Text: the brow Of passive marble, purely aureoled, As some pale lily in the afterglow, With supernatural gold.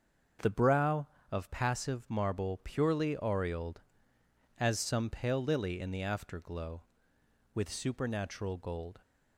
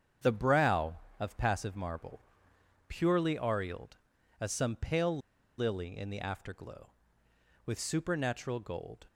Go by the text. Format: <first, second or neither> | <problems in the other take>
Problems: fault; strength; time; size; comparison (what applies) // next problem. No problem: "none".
first | starts louder than the rest; strong; until 1.4 s; 7.5 dB; also in the first // pauses between "pale" and "lily"; at 5.1 s; 0.39 s long